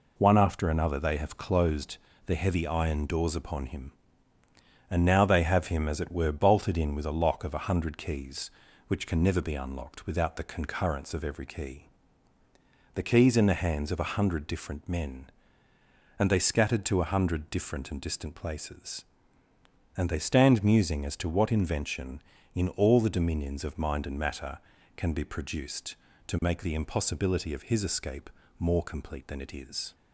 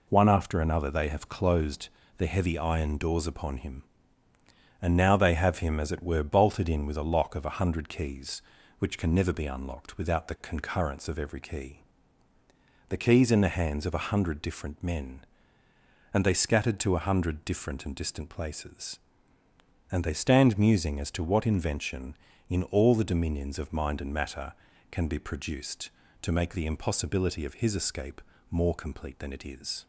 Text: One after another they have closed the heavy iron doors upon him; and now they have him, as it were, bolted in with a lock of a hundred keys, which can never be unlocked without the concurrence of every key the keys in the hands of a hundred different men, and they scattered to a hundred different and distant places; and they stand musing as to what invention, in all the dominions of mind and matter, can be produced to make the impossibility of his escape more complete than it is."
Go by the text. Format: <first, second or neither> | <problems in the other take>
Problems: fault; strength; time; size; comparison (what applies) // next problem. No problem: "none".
neither | pauses between "closed" and "the"; slight; the same in both // pauses between "key" and "the"; the same in both // pauses between "escape" and "more"; slight; the same in both